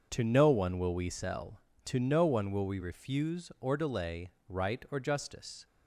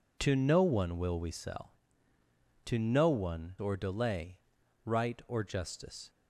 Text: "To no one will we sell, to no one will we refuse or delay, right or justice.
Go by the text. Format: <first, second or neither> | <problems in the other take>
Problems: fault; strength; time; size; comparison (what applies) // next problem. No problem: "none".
first | skips "will we refuse"; at 3.5 s